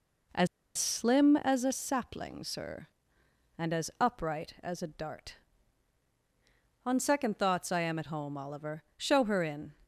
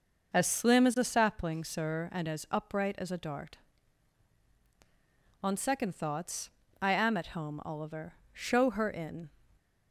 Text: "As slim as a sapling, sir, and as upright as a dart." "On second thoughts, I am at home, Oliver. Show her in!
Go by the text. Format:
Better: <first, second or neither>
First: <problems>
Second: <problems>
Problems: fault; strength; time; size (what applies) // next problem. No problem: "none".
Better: second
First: pauses between "As" and "slim"; slight; at 0.4 s; 0.30 s long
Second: none